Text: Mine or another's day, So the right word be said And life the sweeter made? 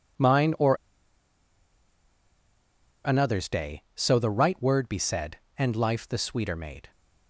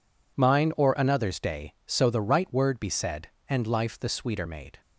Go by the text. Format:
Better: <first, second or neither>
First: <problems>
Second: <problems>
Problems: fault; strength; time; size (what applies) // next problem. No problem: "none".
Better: second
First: pauses between "or" and "another's"; strong; at 0.7 s; 2.3 s long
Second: none